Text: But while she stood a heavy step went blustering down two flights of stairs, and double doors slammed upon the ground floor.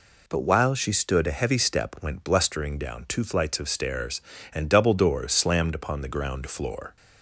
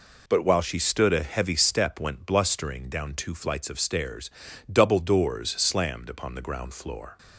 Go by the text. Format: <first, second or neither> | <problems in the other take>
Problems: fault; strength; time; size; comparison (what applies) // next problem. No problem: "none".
first | skips "and"; at 4.5 s